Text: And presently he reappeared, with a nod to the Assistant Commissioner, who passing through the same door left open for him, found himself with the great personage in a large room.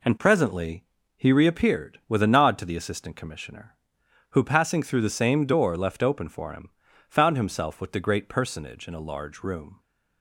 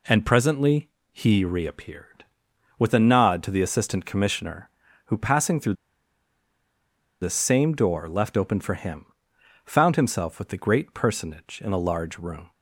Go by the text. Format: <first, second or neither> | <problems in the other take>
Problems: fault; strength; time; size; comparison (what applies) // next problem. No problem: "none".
first | pauses between "presently" and "he"; slight; at 0.8 s; 0.24 s long; slight in the first // pauses between "through" and "the"; strong; at 5.7 s; 1.4 s long